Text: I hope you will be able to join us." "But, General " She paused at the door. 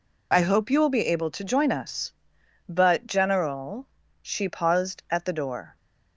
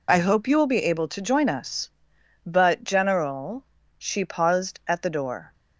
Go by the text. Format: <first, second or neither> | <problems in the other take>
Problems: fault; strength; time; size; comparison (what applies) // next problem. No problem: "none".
neither | none